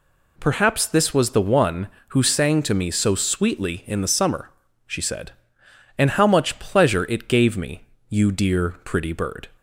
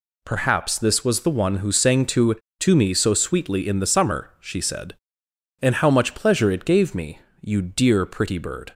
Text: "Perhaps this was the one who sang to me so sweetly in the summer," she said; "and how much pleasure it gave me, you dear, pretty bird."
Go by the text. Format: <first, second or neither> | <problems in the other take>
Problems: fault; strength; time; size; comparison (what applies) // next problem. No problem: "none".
first | says "to" twice; at 2.6 s